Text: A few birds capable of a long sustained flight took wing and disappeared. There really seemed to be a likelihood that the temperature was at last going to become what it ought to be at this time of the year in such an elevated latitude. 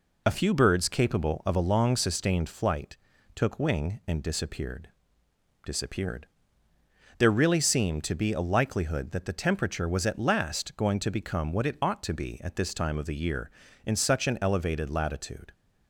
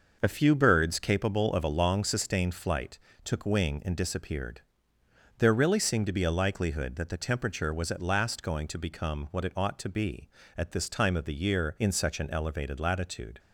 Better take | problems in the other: second | pauses between "flight" and "took"; slight; at 2.9 s; 0.36 s long; slight in the second // says "disappeared" twice; at 5.6 s

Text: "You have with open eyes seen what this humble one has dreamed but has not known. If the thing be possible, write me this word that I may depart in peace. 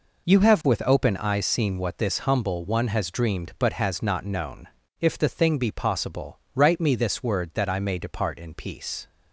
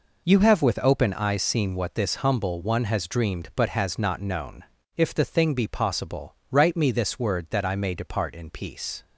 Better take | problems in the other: neither | none

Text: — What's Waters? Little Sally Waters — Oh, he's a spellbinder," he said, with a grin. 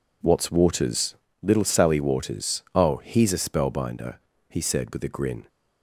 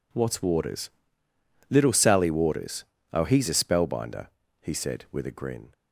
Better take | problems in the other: neither | none

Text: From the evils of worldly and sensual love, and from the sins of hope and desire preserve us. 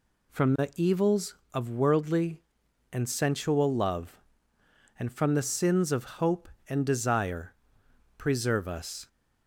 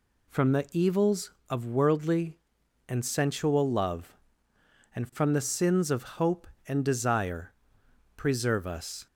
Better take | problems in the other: neither | pauses between "desire" and "preserve"; noticeable; the same in both

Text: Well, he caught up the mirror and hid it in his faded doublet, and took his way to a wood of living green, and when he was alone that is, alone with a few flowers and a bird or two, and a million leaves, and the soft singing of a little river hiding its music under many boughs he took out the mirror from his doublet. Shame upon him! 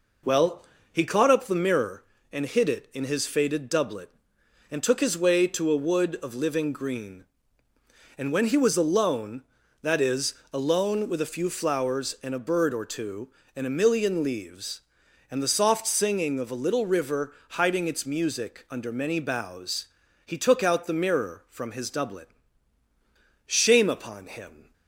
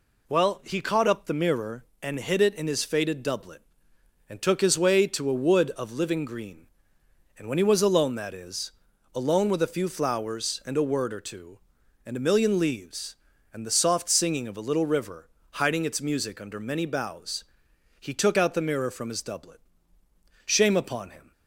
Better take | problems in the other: first | says "word" for "bird"; at 10.8 s // pauses between "river" and "hiding"; slight; at 15.2 s; 0.28 s long; slight in the first // pauses between "boughs" and "he"; noticeable; at 17.4 s; 0.56 s long; slight in the first

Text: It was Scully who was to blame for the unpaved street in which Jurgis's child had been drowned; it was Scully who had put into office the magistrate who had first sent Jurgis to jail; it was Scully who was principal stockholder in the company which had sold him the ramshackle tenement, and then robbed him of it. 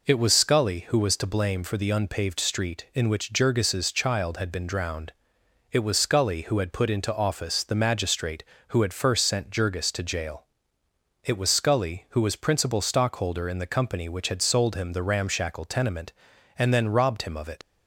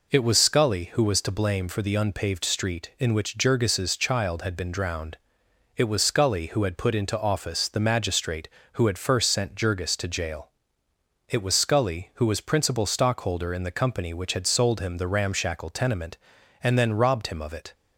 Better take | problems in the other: second | leaves "it" unfinished; at 17.6 s; 80 ms

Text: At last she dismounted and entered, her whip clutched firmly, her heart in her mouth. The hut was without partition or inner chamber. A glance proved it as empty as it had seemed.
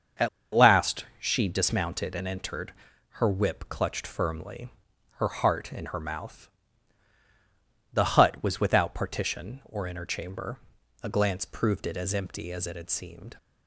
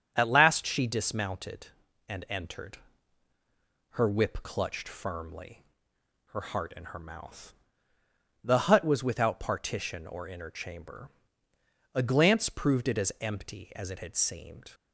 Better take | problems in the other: second | starts louder than the rest; until 1.6 s; 6.5 dB; strong in the second // pauses between "At" and "last"; slight; at 0.2 s; 0.26 s long

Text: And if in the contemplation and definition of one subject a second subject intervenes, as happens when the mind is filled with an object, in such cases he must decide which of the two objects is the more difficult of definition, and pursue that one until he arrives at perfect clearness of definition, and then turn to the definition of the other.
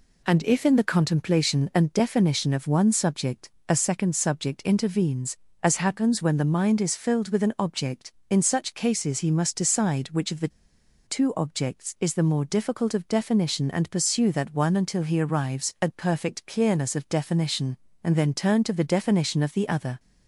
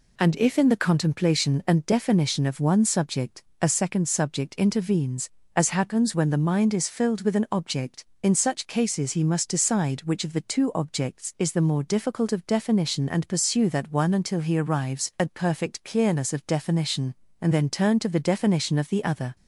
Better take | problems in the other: second | pauses between "subject" and "a"; slight; at 3.5 s; 0.16 s long; slight in the second // pauses between "the" and "two"; noticeable; at 10.4 s; 0.57 s long

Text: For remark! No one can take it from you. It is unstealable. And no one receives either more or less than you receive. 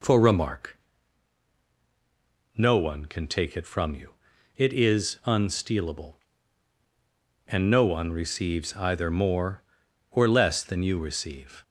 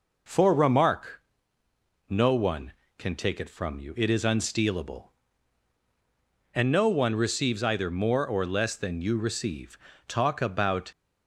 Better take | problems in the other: first | goes on to say "Talk about"; noticeable; from 10.0 s on; 0.82 s long

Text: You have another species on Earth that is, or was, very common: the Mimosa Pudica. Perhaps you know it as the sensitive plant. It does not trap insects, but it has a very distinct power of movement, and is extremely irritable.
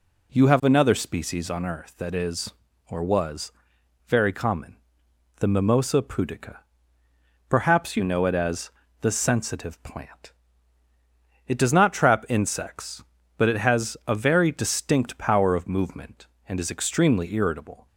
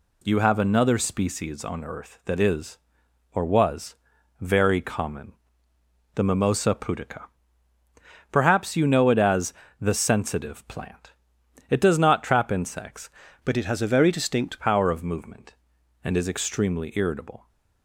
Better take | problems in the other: first | pauses between "as" and "the"; slight; at 9.5 s; 0.28 s long; slight in the first // changes voice from "but" to "distinct"; from 13.4 to 14.6 s; 1.2 s long

